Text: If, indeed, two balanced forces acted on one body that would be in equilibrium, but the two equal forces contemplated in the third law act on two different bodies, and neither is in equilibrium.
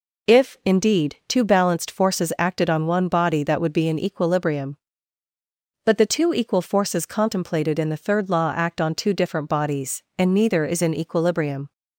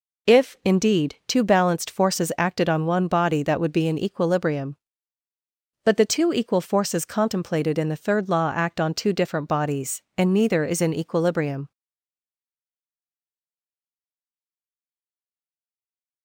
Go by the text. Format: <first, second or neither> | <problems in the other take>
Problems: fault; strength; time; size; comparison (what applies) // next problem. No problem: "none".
first | stays silent after the last word; strong; from 11.7 s on; 4.5 s long